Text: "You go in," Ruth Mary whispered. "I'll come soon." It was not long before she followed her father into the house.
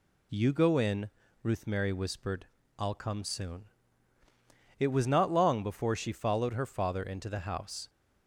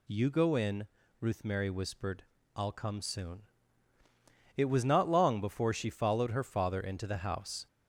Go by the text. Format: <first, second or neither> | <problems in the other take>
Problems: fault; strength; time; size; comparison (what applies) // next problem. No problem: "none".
first | gets louder; slight; throughout; 3 dB